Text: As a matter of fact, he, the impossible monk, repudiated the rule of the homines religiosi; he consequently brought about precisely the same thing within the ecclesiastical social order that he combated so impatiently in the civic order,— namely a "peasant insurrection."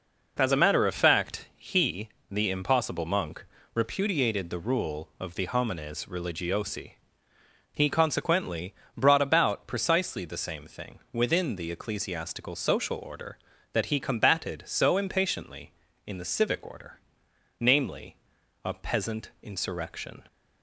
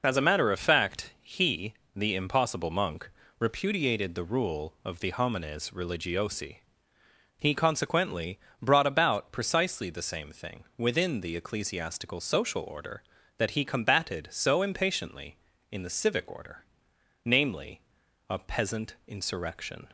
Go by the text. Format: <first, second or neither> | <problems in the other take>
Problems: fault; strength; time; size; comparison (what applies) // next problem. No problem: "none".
first | loses the start of "As"; at 0.0 s; 20 ms // pauses between "consequently" and "brought"; slight; at 8.3 s; 0.24 s long; slight in the first // pauses between "namely" and "a"; noticeable; at 17.8 s; 0.48 s long; noticeable in the first